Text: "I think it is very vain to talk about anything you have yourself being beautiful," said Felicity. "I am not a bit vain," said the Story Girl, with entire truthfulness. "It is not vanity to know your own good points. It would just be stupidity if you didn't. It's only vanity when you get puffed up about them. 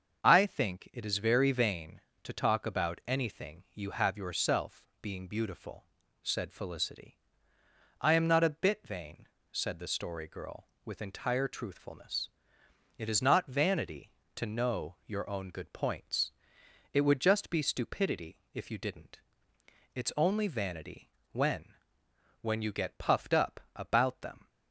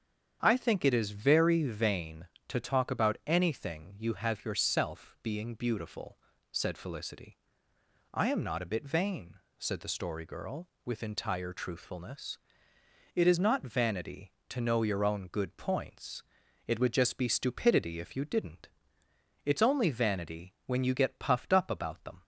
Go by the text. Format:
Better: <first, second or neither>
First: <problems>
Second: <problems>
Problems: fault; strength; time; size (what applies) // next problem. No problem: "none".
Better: second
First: starts louder than the rest; until 1.2 s; 6.5 dB // pauses between "yourself" and "being"; slight; at 4.8 s; 0.16 s long // pauses between "vanity" and "when"; slight; at 21.0 s; 0.22 s long // says "when" twice; at 22.4 s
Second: starts louder than the rest; strong; until 1.4 s; 8 dB